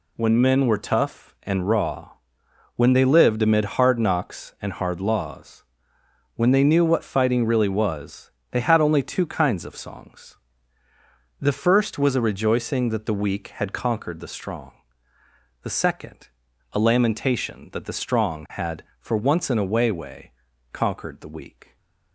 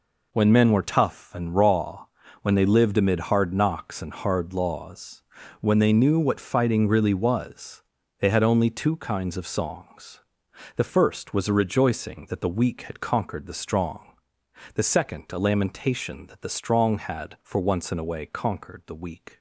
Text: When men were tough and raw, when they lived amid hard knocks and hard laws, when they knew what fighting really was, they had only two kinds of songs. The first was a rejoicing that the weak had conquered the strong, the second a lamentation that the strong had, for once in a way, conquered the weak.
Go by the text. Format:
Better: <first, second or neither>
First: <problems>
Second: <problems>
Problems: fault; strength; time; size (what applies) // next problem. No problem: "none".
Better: second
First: pauses between "second" and "a"; at 16.2 s; 0.44 s long // says "way" twice; at 19.9 s // stays silent after the last word; slight; from 21.6 s on; 0.5 s long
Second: none